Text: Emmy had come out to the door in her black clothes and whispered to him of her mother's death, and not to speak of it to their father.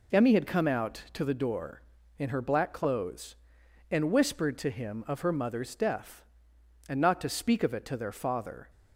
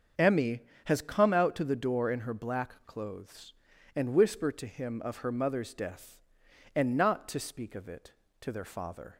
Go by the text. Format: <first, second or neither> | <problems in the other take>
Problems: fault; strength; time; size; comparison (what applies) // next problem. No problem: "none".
first | starts louder than the rest; until 1.4 s; 7 dB // says "has" for "had"; at 0.8 s